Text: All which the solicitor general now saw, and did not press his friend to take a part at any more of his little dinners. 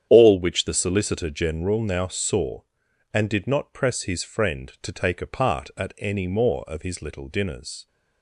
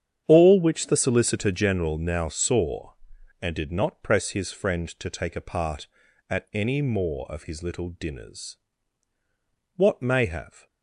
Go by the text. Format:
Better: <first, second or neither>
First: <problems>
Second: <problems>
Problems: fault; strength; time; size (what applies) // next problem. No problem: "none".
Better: first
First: starts louder than the rest; strong; until 1.1 s; 9 dB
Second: starts louder than the rest; strong; until 1.2 s; 8.5 dB // goes on to say "What may have"; noticeable; from 9.7 s on; 0.90 s long